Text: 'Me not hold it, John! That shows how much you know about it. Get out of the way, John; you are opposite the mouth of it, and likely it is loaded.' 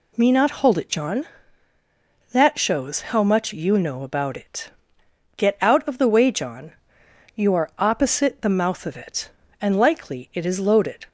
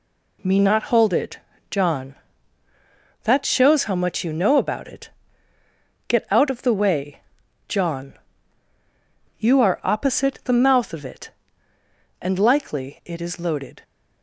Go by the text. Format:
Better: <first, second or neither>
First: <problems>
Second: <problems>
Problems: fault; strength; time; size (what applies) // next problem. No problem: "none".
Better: neither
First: none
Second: none